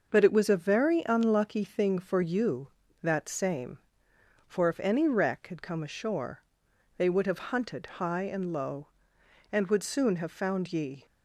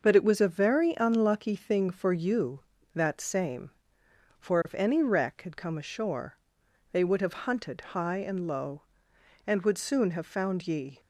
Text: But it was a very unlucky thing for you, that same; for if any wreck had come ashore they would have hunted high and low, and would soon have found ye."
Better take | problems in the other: neither | starts louder than the rest; noticeable; the same in both // pauses between "ashore" and "they"; noticeable; the same in both

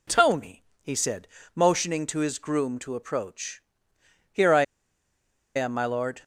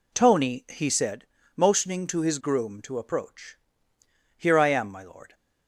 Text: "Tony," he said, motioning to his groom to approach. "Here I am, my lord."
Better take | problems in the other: second | pauses between "I" and "am"; noticeable; at 4.6 s; 0.93 s long

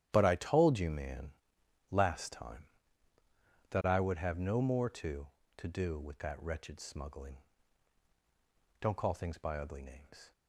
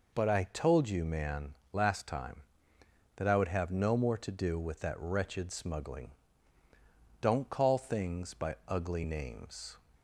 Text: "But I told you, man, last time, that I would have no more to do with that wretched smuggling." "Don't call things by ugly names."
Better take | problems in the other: second | starts louder than the rest; strong; until 1.1 s; 11.5 dB // says "to" twice; at 5.5 s

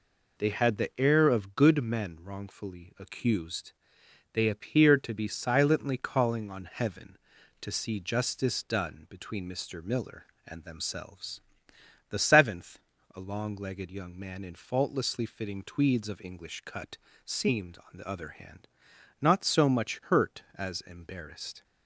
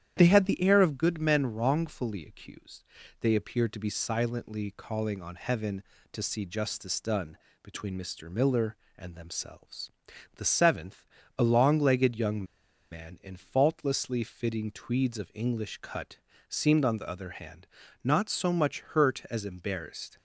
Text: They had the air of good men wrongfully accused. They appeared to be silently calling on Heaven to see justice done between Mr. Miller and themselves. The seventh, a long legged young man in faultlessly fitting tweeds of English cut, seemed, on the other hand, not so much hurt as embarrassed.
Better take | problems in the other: first | starts louder than the rest; strong; until 1.1 s; 10 dB // pauses between "done" and "between"; slight; at 7.3 s; 0.24 s long // pauses between "young" and "man"; noticeable; at 12.4 s; 0.47 s long

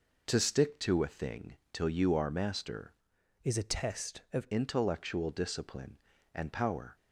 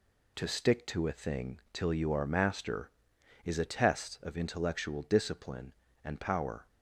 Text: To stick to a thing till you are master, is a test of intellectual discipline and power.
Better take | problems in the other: second | pauses between "thing" and "till"; slight; at 1.5 s; 0.16 s long // changes voice from "is" to "of"; from 3.4 to 4.4 s; 1.0 s long

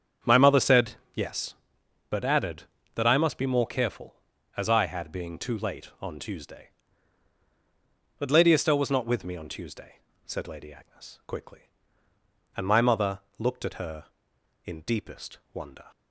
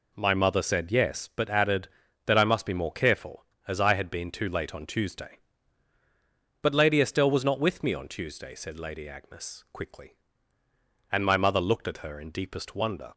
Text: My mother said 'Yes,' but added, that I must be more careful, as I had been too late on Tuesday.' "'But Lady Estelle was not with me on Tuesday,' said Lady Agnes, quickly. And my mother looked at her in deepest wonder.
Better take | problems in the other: second | starts louder than the rest; strong; until 1.4 s; 8 dB // pauses between "said" and "Yes"; slight; at 0.9 s; 0.18 s long // says "being" for "been"; at 5.1 s // pauses between "mother" and "looked"; slight; at 13.1 s; 0.20 s long // pauses between "deepest" and "wonder"; slight; at 15.3 s; 0.16 s long

